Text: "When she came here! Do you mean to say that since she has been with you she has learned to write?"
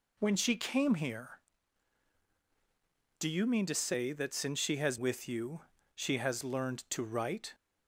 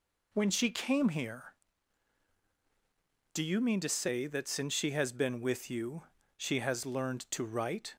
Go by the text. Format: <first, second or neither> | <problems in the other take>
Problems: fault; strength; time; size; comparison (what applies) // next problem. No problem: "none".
second | skips "been"; at 4.9 s // pauses between "you" and "she"; slight; at 5.6 s; 0.32 s long; slight in the second